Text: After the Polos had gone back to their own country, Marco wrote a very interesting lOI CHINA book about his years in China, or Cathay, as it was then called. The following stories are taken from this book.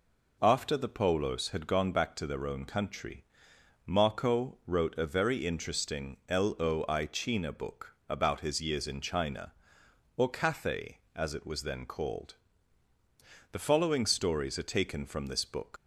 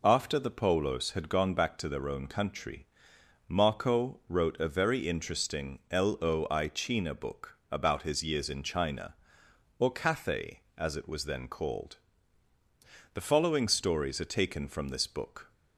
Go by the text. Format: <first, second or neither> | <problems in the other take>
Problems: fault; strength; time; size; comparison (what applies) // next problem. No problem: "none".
second | leaves "book" unfinished; at 15.7 s; 140 ms